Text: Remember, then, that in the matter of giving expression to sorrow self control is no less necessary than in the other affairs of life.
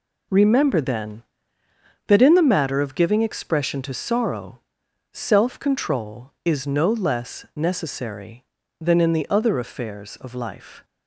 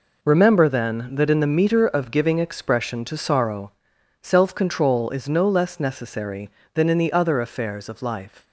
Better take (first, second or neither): first